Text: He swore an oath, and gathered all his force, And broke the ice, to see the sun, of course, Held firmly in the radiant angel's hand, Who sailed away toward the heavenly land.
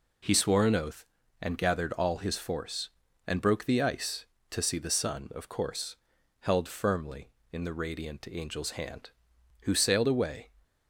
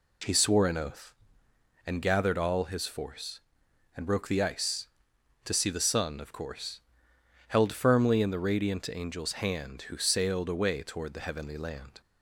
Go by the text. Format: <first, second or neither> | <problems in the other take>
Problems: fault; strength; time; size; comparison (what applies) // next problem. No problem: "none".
second | stops before "toward the heavenly land"; at 10.6 s